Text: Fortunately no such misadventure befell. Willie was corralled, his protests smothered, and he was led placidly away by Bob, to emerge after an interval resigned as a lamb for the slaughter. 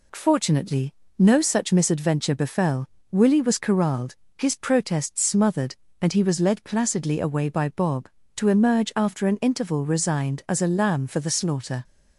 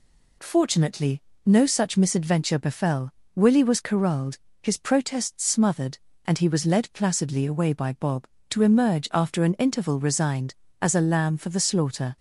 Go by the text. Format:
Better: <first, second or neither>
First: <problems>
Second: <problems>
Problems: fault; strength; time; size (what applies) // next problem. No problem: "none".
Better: neither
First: pauses between "Fortunately" and "no"; slight; at 0.9 s; 0.28 s long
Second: pauses between "Fortunately" and "no"; slight; at 1.2 s; 0.28 s long